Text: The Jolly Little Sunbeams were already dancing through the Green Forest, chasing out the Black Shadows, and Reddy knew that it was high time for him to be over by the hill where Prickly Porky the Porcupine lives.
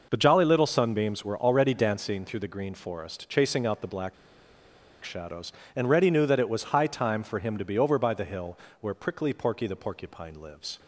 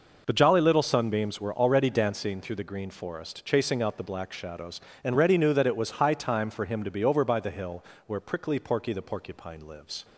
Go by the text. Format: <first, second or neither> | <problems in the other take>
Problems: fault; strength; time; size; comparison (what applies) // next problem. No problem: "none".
second | pauses between "Black" and "Shadows"; noticeable; at 4.1 s; 0.89 s long // pauses between "hill" and "where"; slight; at 8.5 s; 0.24 s long; slight in the second